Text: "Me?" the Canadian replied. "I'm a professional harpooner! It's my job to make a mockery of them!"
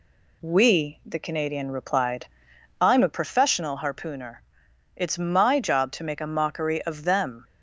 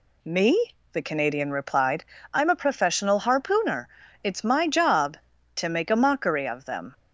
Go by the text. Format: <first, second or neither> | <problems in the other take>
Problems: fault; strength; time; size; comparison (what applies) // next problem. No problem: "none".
second | says "We" for "Me"; at 0.4 s